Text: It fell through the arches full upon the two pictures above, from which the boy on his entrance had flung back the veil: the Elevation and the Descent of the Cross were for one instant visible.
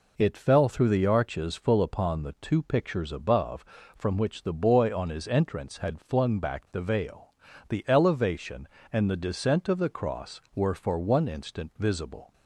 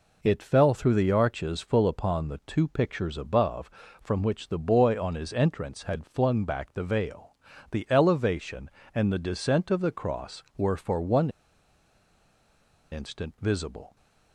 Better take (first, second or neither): first